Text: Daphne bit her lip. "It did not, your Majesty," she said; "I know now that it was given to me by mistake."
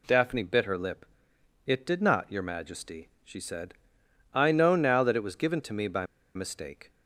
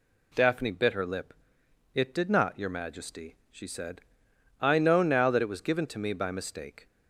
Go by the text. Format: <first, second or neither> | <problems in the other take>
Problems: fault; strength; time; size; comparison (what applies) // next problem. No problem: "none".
second | pauses between "by" and "mistake"; slight; at 6.0 s; 0.30 s long